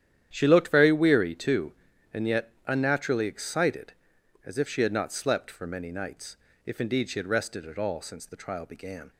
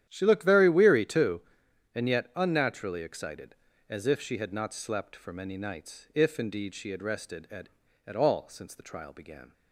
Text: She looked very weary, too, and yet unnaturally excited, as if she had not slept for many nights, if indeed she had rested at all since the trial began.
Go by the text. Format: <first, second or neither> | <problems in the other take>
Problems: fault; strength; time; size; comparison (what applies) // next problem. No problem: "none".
first | starts louder than the rest; strong; until 1.0 s; 10.5 dB; strong in the first // says "at" twice; at 8.0 s